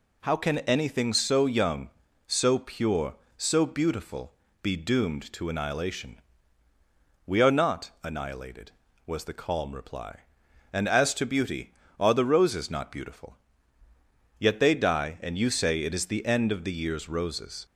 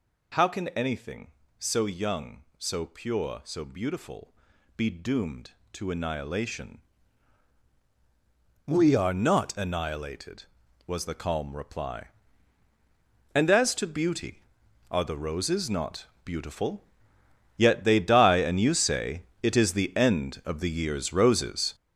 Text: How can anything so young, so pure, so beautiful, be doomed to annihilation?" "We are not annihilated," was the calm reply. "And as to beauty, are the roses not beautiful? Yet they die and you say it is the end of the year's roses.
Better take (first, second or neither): first